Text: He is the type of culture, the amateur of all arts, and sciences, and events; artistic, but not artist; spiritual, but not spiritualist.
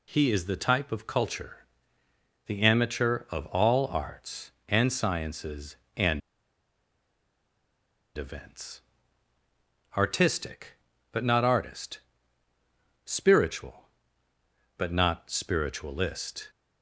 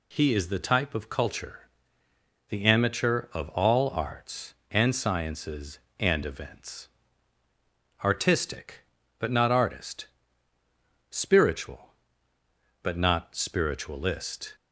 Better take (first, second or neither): second